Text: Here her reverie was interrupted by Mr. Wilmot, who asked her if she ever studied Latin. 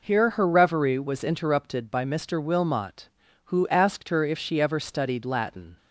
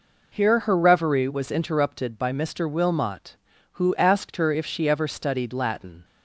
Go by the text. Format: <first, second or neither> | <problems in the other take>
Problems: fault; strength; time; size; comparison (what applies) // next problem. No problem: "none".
neither | none